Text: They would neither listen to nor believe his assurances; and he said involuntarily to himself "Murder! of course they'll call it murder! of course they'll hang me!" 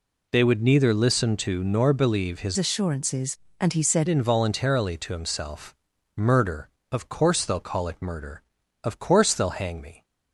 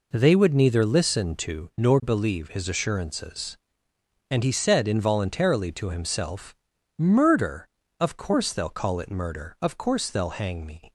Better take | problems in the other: second | changes voice from "assurances" to "said"; from 2.5 to 4.0 s; 1.5 s long // pauses between "himself" and "Murder"; at 5.7 s; 0.40 s long; also in the second

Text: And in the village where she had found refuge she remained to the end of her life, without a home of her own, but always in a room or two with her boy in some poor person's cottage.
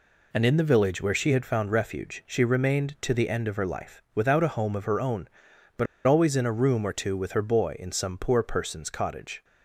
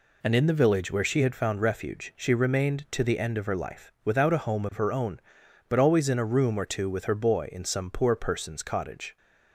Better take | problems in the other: second | pauses between "but" and "always"; slight; at 5.8 s; 0.21 s long

